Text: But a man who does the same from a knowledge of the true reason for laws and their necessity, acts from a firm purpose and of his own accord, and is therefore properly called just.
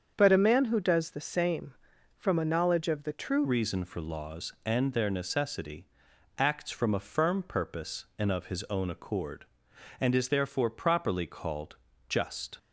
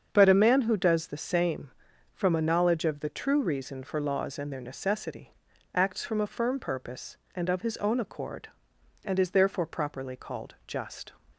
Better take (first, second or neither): second